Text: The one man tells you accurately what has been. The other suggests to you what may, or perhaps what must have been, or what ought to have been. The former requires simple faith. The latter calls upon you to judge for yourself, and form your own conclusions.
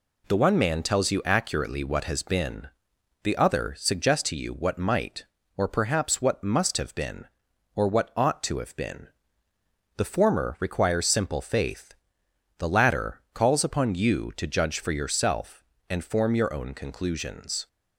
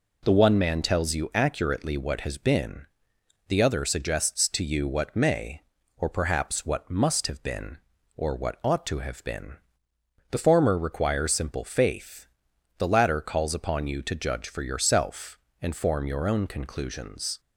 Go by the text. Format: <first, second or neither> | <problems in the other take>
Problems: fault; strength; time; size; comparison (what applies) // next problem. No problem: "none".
second | says "might" for "may"; at 4.7 s